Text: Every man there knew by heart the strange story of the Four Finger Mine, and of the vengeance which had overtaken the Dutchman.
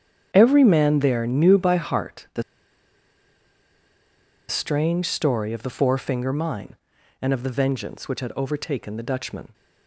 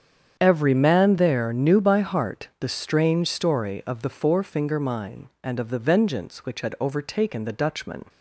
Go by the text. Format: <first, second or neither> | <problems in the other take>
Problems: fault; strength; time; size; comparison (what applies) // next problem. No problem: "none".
second | starts louder than the rest; strong; until 1.3 s; 8.5 dB; strong in the second // pauses between "the" and "strange"; strong; at 2.4 s; 2.0 s long